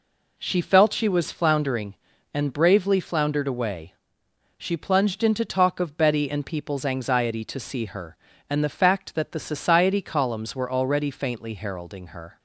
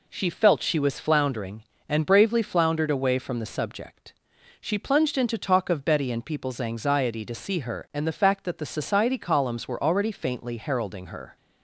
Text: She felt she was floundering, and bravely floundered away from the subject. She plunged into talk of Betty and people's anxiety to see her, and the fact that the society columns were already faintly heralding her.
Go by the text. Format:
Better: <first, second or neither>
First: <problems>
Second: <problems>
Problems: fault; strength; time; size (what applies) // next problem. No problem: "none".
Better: second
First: skips "from the subject"; at 4.2 s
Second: none